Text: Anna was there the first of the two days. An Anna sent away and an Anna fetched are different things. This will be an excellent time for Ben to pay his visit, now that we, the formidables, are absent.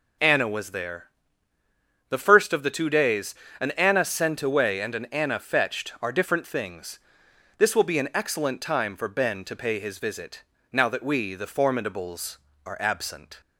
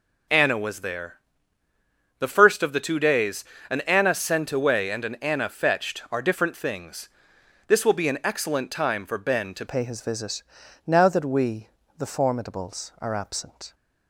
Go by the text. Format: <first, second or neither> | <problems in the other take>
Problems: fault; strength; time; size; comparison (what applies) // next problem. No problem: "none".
first | pauses between "there" and "the"; at 1.1 s; 1.0 s long; also in the first // changes voice at "pay"; from 9.6 s on; 4.1 s long